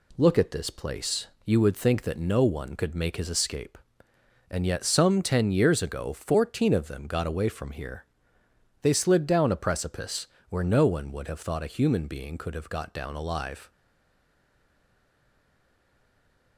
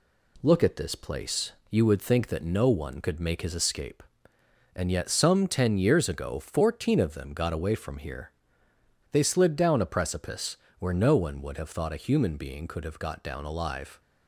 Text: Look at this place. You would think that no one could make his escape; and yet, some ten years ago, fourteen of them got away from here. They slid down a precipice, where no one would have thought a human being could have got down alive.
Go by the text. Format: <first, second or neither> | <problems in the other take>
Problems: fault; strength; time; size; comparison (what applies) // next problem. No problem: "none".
second | stays silent after the last word; strong; from 13.7 s on; 2.8 s long